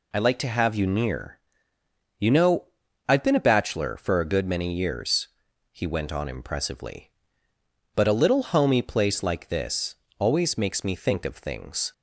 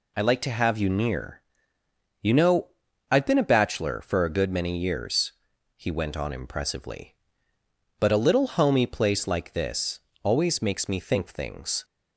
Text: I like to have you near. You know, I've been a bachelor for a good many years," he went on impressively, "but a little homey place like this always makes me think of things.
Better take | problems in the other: first | pauses between "this" and "always"; slight; at 10.0 s; 0.24 s long; slight in the first // skips "of"; at 11.2 s

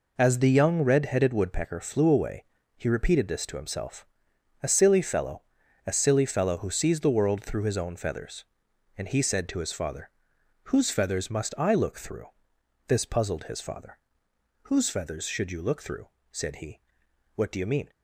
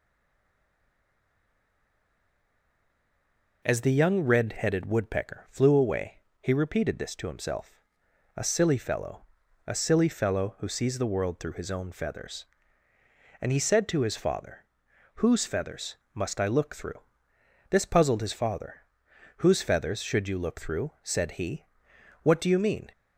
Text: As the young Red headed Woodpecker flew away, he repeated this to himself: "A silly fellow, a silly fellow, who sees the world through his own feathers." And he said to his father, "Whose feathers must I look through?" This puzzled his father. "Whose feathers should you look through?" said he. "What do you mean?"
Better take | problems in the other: first | stays silent before the first word; strong; until 3.6 s; 3.6 s long // pauses between "feathers" and "must"; slight; at 15.9 s; 0.18 s long

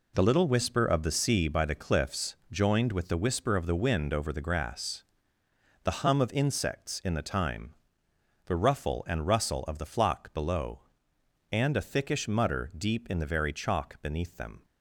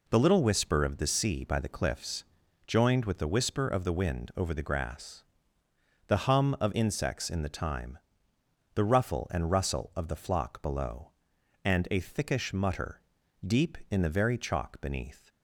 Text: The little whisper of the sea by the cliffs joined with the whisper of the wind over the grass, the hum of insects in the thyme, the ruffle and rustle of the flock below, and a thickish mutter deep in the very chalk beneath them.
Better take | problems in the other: first | pauses between "cliffs" and "joined"; noticeable; at 2.2 s; 0.46 s long; slight in the first // pauses between "mutter" and "deep"; at 13.0 s; 0.44 s long // stops before "them"; at 15.2 s

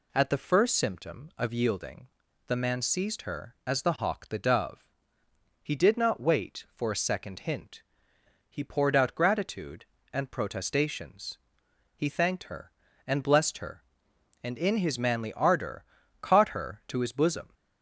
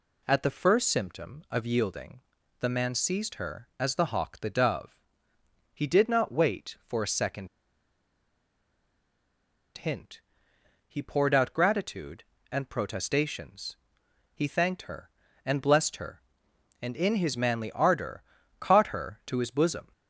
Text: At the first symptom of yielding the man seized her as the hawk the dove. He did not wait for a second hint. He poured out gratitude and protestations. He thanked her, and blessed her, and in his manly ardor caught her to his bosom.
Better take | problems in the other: first | pauses between "yielding" and "the"; at 2.2 s; 0.40 s long; also in the first // pauses between "second" and "hint"; strong; at 7.4 s; 2.2 s long // pauses between "ardor" and "caught"; slight; at 18.2 s; 0.34 s long; slight in the first

